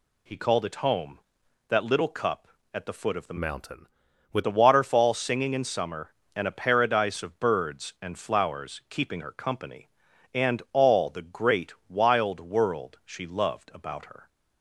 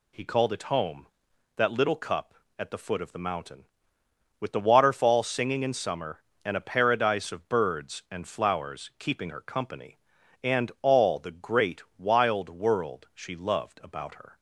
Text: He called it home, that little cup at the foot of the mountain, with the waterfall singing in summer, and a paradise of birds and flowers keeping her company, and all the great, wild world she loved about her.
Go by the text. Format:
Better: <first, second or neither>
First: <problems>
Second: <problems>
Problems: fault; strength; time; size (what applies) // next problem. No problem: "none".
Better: second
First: changes voice from "mountain" to "with"; from 3.3 to 4.4 s; 1.1 s long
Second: none